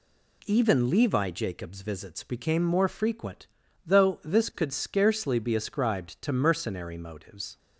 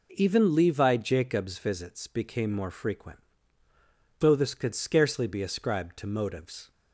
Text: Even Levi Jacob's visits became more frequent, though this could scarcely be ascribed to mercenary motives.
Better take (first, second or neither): first